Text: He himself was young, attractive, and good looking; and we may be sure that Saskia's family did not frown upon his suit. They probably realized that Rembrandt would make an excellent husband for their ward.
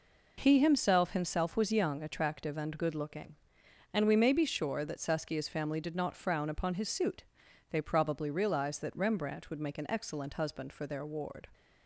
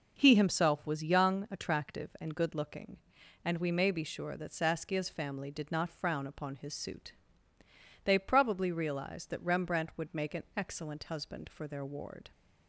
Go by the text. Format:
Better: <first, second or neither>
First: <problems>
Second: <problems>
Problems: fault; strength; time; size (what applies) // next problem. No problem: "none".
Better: second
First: says "himself" twice; at 1.1 s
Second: none